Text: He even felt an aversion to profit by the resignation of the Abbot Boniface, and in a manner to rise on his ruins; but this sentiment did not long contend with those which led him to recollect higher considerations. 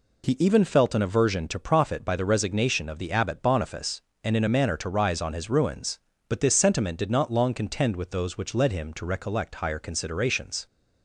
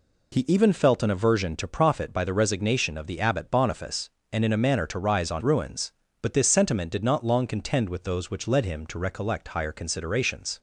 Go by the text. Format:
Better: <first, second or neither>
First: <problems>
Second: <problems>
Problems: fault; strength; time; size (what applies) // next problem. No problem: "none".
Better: first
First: none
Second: skips "his"; at 5.4 s